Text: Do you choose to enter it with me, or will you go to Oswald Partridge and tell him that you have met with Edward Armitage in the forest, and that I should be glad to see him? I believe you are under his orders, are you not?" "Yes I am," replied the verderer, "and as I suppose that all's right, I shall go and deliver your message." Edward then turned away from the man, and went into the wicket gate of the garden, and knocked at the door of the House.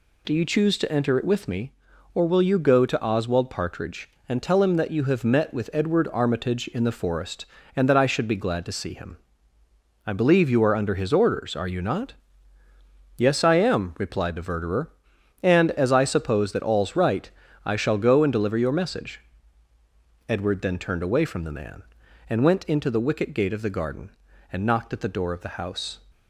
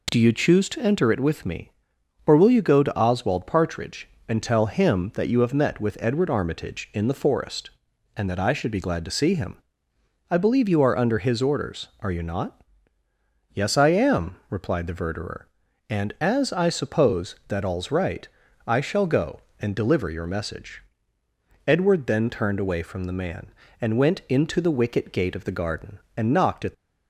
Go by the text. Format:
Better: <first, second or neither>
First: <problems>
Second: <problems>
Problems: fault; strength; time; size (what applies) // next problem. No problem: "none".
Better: first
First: none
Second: stops before "the door of the House"; at 26.7 s